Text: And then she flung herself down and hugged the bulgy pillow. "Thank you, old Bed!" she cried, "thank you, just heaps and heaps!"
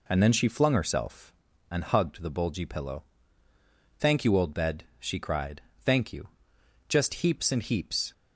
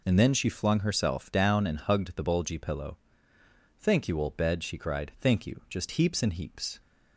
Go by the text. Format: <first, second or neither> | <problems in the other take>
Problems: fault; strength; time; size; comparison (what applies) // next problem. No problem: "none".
second | skips "down"; at 1.5 s